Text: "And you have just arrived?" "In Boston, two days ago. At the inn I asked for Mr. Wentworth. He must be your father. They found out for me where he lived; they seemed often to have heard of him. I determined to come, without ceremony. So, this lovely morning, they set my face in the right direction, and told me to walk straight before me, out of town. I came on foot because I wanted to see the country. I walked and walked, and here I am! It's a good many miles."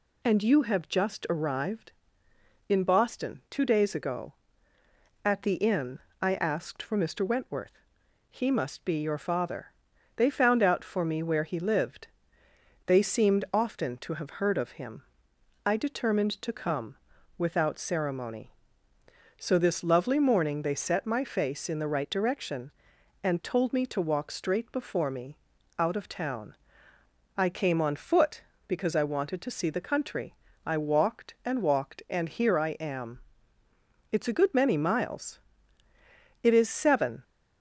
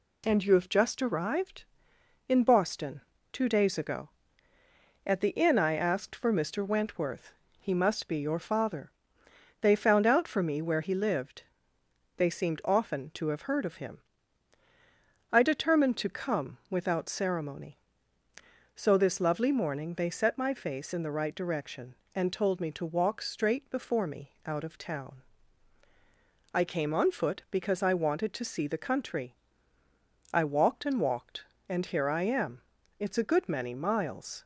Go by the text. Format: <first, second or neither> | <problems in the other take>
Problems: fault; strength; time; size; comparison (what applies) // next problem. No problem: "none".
second | pauses between "inn" and "I"; slight; at 5.9 s; 0.22 s long // goes on to say "It is seven"; noticeable; from 36.4 s on; 0.82 s long